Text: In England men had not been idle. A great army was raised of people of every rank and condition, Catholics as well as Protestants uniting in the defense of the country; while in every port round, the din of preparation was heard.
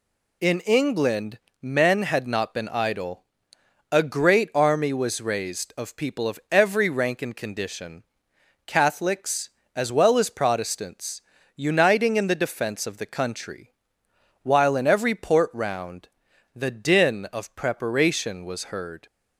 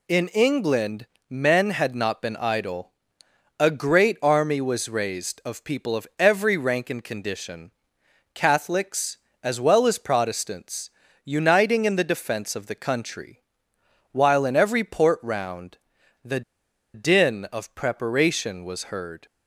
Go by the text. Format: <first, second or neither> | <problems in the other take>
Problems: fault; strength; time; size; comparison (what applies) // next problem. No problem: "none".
first | pauses between "England" and "men"; slight; at 1.0 s; 0.22 s long; slight in the first // pauses between "Protestants" and "uniting"; slight; at 10.8 s; 0.36 s long; slight in the first // pauses between "the" and "din"; noticeable; at 16.4 s; 0.53 s long